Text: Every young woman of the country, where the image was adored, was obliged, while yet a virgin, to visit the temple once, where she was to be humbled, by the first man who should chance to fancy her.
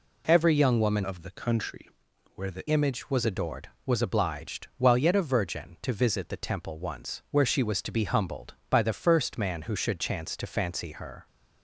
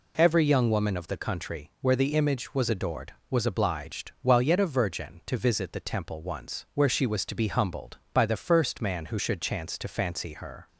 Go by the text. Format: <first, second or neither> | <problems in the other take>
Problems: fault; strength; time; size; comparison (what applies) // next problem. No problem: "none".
second | changes voice from "of" to "the"; from 1.0 to 2.6 s; 1.6 s long